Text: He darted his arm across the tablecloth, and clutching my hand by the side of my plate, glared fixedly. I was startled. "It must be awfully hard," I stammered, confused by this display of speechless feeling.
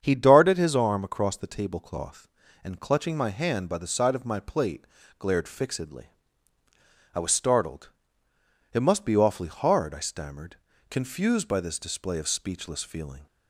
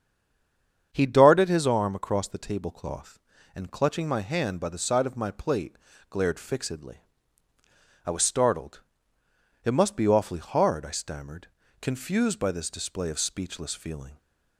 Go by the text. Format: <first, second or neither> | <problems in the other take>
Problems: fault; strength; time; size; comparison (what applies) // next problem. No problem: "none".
first | stays silent before the first word; slight; until 0.9 s; 0.9 s long // starts louder than the rest; strong; until 1.9 s; 7.5 dB; strong in the first